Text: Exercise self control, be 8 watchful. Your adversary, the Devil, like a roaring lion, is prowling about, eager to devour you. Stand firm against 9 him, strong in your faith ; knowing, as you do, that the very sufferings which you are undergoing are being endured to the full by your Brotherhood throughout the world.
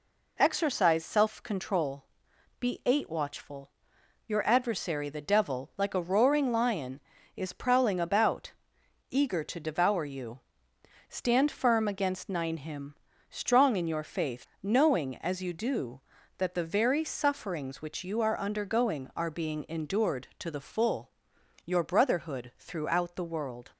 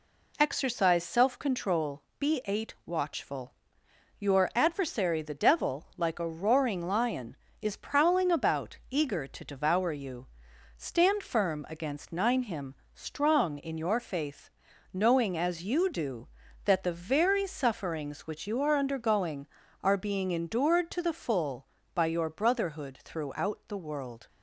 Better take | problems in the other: second | skips "by"; at 21.3 s

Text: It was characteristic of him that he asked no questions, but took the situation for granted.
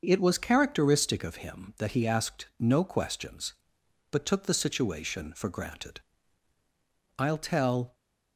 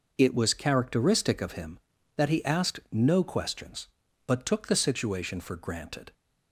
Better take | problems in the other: second | starts louder than the rest; until 1.0 s; 6.5 dB // goes on to say "I'll tell"; noticeable; from 7.1 s on; 0.76 s long

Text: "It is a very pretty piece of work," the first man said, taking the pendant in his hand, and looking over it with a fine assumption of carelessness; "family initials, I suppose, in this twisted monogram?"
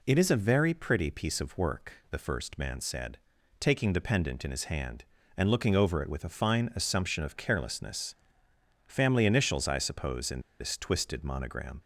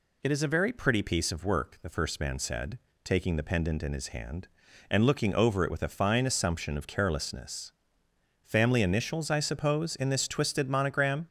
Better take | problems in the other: second | pauses between "in" and "this"; slight; at 10.3 s; 0.20 s long

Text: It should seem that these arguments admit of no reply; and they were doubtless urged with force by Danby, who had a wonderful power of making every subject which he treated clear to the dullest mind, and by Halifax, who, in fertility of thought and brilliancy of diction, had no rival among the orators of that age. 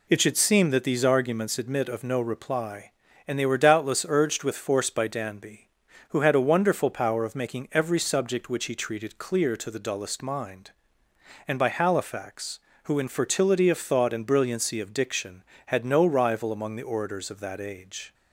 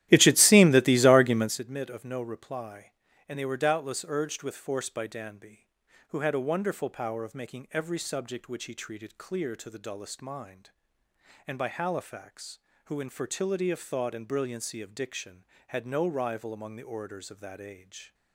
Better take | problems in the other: first | starts louder than the rest; strong; until 1.6 s; 13.5 dB

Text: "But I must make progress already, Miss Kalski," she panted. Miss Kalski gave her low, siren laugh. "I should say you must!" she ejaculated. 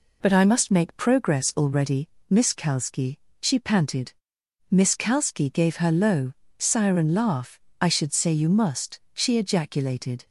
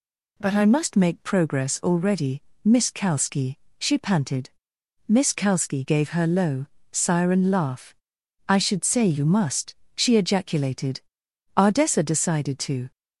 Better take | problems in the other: first | goes on to say "Ardessa decided to"; from 11.5 s on; 1.3 s long

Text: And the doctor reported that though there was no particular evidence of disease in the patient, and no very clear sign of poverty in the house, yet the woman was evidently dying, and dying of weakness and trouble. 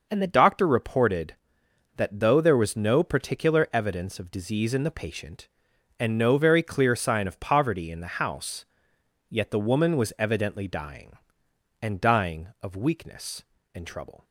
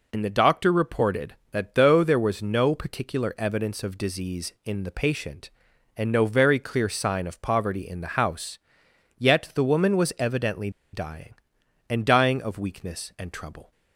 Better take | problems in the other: first | pauses between "evidently" and "dying"; slight; at 10.7 s; 0.22 s long

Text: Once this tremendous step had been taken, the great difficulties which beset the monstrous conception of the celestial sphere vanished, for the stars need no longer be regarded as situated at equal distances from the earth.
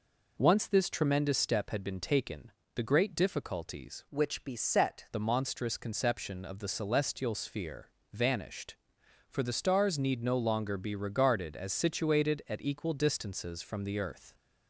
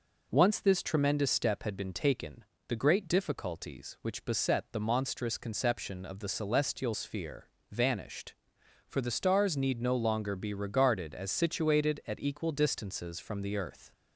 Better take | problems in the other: second | changes voice from "which" to "beset"; from 4.0 to 5.0 s; 1.0 s long // pauses between "sphere" and "vanished"; slight; at 7.8 s; 0.24 s long; slight in the second

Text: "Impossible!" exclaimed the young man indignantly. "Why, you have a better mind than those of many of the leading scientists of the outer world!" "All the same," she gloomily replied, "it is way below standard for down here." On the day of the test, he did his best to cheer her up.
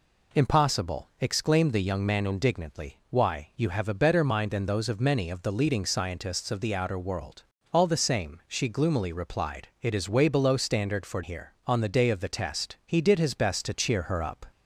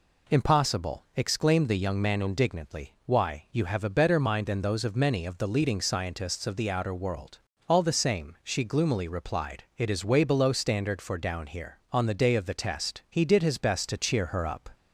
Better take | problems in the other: second | skips "down"; at 11.2 s

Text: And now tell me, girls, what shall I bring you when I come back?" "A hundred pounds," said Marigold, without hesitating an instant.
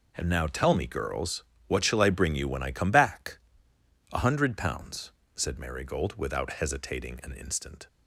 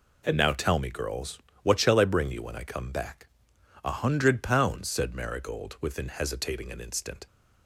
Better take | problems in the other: first | says "within" for "without"; at 5.8 s

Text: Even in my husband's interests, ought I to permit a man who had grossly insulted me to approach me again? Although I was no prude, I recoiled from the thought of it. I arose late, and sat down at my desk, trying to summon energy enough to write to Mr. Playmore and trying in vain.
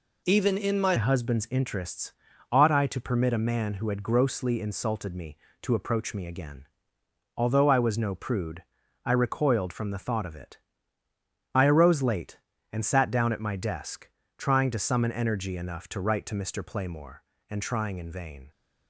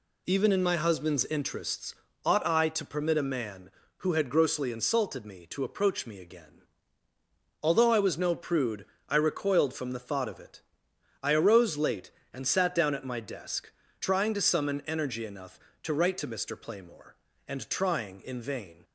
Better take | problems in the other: second | changes voice at "husband's"; from 0.9 s on; 17.5 s long

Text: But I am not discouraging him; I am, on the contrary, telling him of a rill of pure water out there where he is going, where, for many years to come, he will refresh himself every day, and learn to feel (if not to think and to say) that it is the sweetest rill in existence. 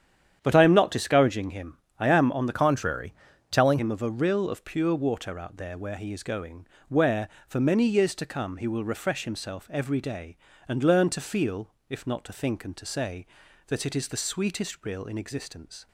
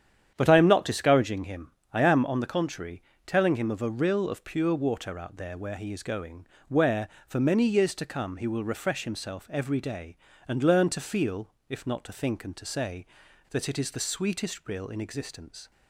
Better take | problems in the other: second | starts louder than the rest; strong; until 1.4 s; 9 dB; strong in the second // changes voice from "contrary" to "telling"; from 2.5 to 3.7 s; 1.2 s long

